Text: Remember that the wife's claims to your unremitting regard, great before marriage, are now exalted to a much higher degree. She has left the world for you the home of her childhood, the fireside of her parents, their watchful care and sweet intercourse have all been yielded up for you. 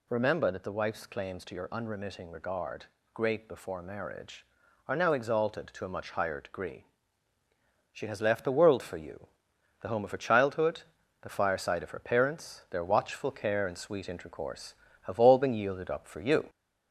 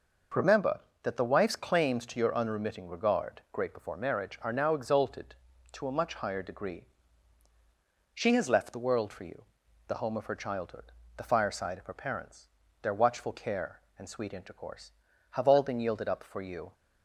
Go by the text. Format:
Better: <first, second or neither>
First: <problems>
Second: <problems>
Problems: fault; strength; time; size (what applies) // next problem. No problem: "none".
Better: second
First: gets louder; slight; throughout; 2 dB // pauses between "you" and "the"; noticeable; at 9.2 s; 0.54 s long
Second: pauses between "you" and "the"; noticeable; at 9.4 s; 0.46 s long